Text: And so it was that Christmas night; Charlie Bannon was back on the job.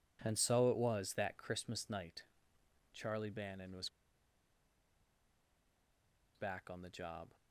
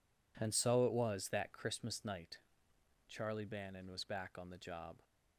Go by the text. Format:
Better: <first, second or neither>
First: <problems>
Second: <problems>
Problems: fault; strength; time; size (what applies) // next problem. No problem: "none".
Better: second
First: pauses between "was" and "back"; strong; at 3.8 s; 2.4 s long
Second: none